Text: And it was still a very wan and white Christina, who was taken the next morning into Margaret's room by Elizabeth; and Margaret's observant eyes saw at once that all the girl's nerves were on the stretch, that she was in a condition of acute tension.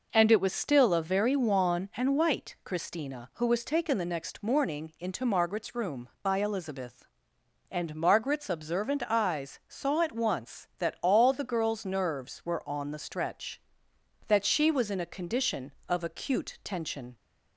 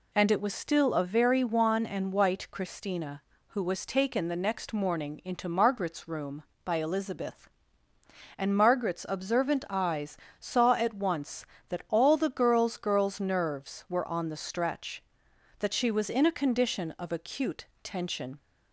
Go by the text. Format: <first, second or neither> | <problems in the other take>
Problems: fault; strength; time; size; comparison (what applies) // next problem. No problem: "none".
first | pauses between "eyes" and "saw"; slight; at 10.1 s; 0.20 s long // says "girl's" twice; at 12.7 s // pauses between "acute" and "tension"; slight; at 17.6 s; 0.18 s long